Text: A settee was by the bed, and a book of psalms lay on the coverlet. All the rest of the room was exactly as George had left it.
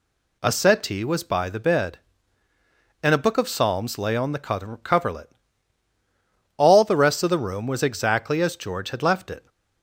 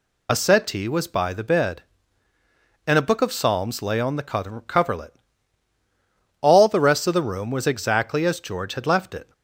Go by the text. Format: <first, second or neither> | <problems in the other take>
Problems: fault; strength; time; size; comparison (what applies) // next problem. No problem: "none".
first | loses the start of "A"; at 0.2 s; 50 ms